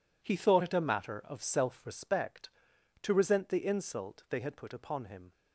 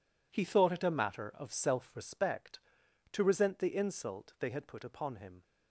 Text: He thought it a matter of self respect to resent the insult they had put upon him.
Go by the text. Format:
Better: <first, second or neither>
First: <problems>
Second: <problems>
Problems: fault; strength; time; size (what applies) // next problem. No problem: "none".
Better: neither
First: none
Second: none